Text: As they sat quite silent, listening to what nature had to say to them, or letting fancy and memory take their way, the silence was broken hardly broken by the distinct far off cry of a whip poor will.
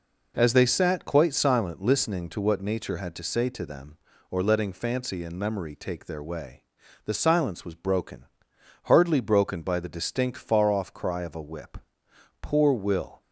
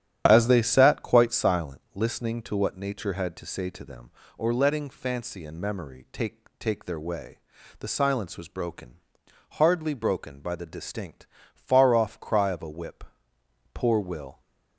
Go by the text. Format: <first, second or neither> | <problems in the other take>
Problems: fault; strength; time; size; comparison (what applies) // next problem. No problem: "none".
first | starts louder than the rest; strong; until 1.2 s; 10 dB // says "take" twice; at 6.5 s // pauses between "broken" and "hardly"; noticeable; at 8.9 s; 0.54 s long; noticeable in the first // pauses between "distinct" and "far"; slight; at 11.2 s; 0.28 s long // pauses between "whip" and "poor"; noticeable; at 13.0 s; 0.68 s long; noticeable in the first